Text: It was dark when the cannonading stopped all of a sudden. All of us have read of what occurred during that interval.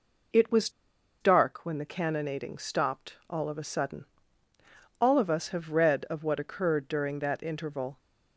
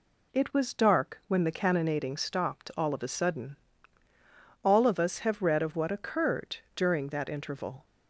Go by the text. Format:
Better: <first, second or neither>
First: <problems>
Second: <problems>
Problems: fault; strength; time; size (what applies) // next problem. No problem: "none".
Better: second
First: pauses between "was" and "dark"; noticeable; at 0.6 s; 0.51 s long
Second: none